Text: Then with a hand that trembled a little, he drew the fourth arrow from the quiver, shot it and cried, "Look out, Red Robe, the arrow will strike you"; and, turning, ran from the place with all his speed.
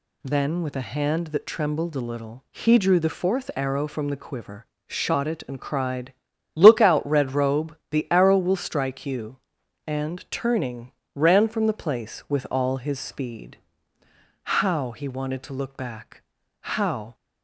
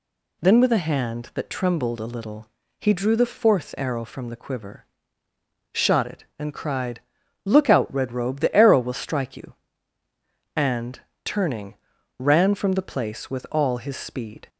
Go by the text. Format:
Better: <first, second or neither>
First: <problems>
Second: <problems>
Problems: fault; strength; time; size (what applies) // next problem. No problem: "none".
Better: second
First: goes on to say "How he wanted to look back How"; strong; from 14.4 s on; 2.7 s long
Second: none